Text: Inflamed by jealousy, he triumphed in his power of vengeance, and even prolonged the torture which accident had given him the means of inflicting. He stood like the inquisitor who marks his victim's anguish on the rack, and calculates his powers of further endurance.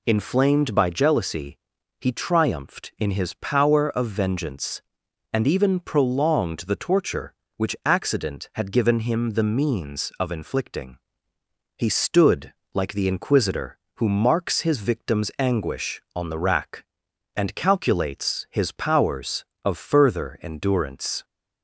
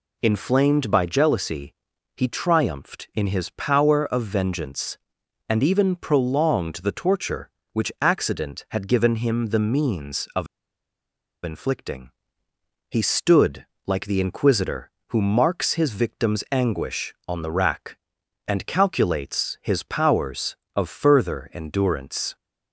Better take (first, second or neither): first